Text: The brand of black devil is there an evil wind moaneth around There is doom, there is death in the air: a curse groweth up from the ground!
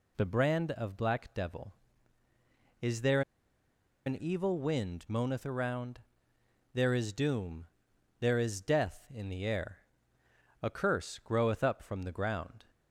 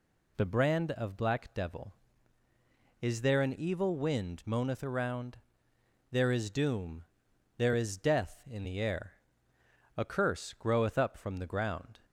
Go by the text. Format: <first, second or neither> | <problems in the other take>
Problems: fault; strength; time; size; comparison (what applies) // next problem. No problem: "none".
second | pauses between "there" and "an"; noticeable; at 3.2 s; 0.85 s long // pauses between "around" and "There"; noticeable; at 5.9 s; 0.74 s long; noticeable in the second